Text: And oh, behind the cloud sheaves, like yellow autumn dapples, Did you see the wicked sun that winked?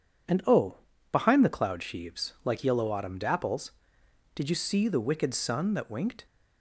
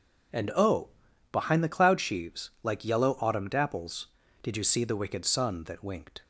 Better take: neither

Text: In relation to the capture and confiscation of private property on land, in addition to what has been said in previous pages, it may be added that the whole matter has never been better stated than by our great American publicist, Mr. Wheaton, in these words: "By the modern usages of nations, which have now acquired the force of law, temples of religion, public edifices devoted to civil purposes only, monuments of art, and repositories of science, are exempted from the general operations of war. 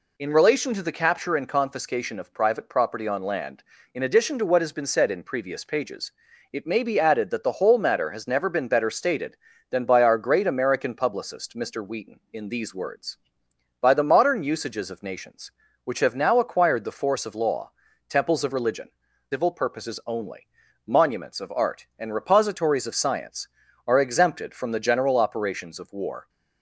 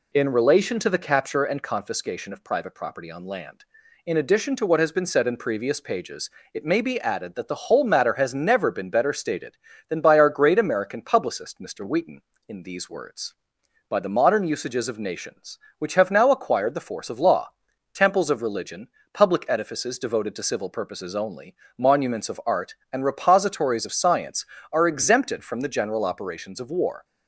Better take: second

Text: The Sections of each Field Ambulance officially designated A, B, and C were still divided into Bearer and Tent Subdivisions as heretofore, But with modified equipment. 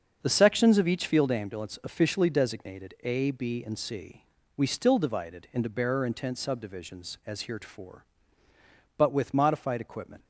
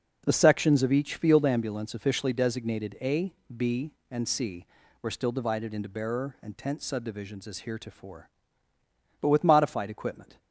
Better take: second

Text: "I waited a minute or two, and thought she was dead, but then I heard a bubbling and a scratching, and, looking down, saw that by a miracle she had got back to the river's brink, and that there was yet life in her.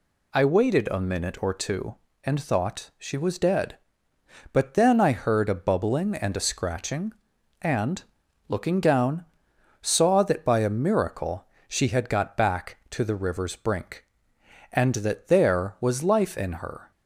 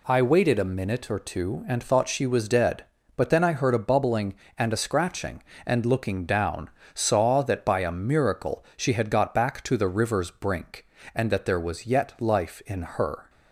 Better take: second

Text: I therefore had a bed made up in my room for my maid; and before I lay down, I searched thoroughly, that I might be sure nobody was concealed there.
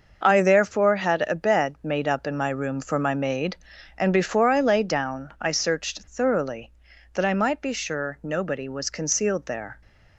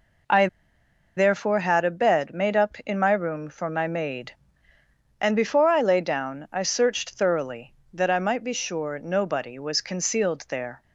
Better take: first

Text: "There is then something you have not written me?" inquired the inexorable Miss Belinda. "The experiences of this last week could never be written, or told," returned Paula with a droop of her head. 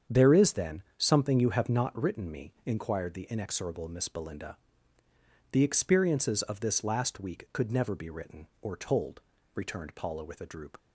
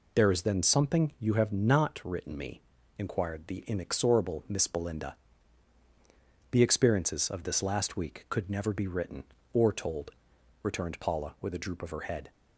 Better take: second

